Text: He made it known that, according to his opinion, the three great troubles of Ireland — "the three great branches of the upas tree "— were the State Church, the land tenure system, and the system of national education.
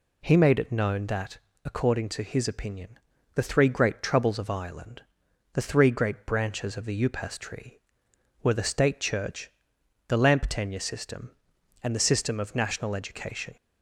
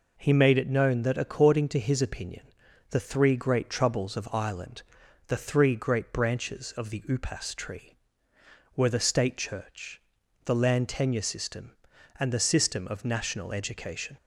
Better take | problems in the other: second | says "lamp" for "land"; at 10.1 s

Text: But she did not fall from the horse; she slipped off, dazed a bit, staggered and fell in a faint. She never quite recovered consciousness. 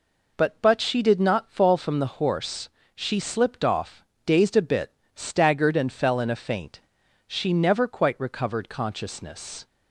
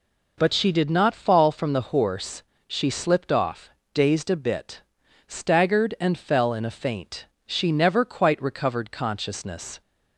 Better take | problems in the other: second | says "But" twice; at 0.6 s

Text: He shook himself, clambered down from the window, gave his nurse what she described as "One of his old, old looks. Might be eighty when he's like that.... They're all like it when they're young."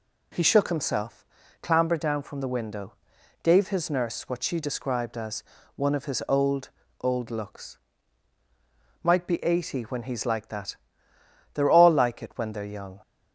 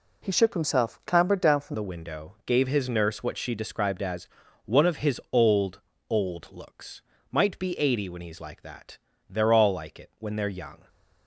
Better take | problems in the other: first | changes voice at "the"; from 1.7 s on; 9.1 s long // pauses between "as" and "One"; at 4.2 s; 0.38 s long; slight in the first

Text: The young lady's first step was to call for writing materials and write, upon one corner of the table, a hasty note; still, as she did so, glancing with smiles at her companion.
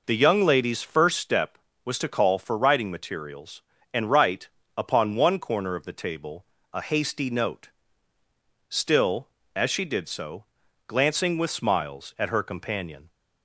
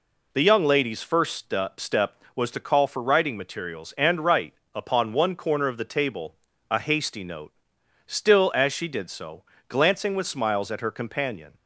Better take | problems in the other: first | says "step" twice; at 1.8 s

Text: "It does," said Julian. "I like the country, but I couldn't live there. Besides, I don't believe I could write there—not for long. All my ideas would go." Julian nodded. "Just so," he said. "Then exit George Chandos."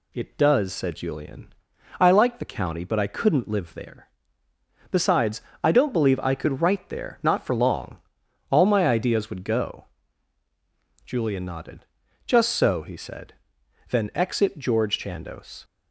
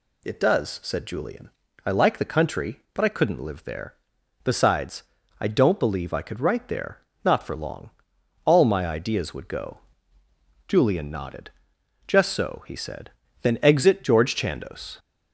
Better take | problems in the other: second | says "county" for "country"; at 2.4 s

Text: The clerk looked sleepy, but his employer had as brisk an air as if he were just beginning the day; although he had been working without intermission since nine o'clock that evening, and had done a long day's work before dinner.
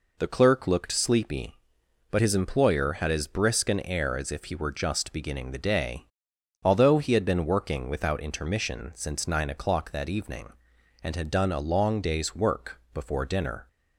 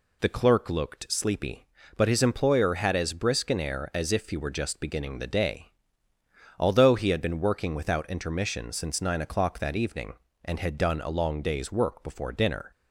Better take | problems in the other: neither | none

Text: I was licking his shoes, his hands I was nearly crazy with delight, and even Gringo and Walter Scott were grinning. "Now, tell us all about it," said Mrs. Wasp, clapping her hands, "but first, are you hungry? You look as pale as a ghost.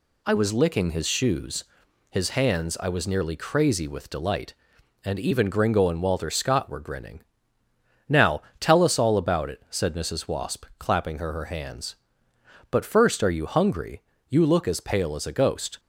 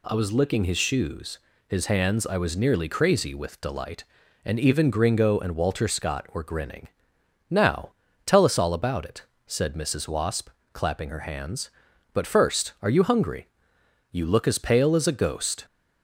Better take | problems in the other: second | says "her" twice; at 11.3 s

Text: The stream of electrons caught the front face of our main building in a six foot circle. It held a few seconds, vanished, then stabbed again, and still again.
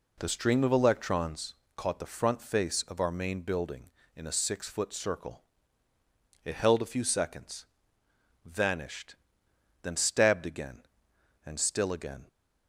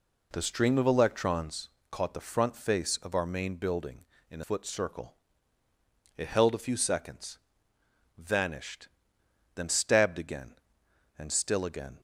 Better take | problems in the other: first | pauses between "electrons" and "caught"; slight; at 1.6 s; 0.22 s long; slight in the first // skips "six"; at 4.4 s

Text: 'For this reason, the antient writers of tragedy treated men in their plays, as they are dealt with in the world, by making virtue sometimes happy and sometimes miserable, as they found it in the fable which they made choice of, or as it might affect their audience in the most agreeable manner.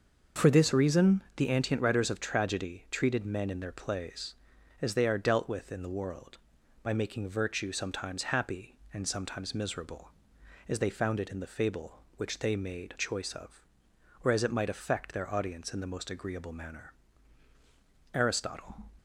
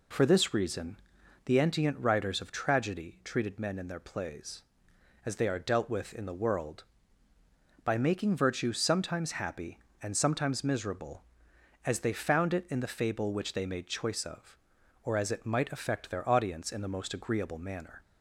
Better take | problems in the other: second | starts louder than the rest; noticeable; until 1.5 s; 6 dB // goes on to say "Aristotle"; noticeable; from 18.1 s on; 0.78 s long

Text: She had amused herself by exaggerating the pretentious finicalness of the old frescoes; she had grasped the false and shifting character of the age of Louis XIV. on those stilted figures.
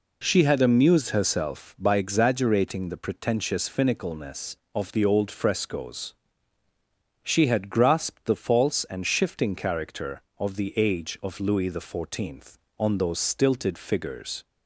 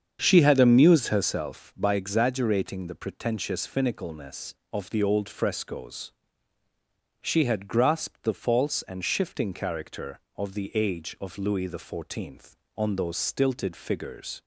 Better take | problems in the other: first | starts louder than the rest; strong; until 1.2 s; 7.5 dB

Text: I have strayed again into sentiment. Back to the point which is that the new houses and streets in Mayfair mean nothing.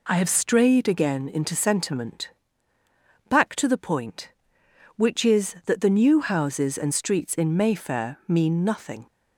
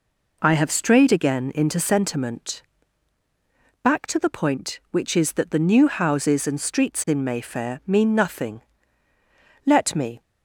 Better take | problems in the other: first | goes on to say "Let me"; from 9.6 s on; 0.54 s long

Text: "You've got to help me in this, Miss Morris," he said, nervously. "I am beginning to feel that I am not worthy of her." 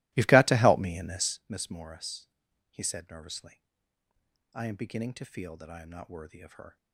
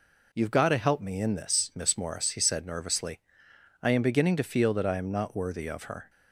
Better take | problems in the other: second | starts louder than the rest; strong; until 1.4 s; 20.5 dB

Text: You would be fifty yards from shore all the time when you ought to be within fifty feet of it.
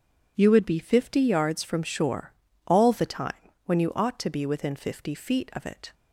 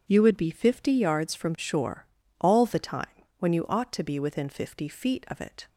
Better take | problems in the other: neither | pauses between "shore" and "all"; slight; the same in both // pauses between "time" and "when"; slight; the same in both

